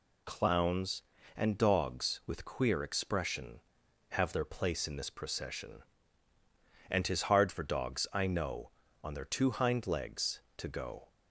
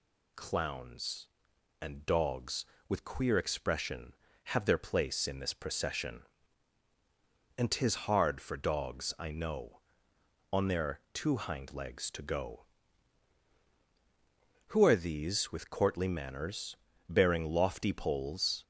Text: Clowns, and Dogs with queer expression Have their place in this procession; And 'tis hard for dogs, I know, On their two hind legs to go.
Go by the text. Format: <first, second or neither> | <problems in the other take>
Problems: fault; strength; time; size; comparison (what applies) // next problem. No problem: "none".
first | goes on to say "Who are these with courtly manners Bearing lofty poles"; strong; from 14.6 s on; 3.9 s long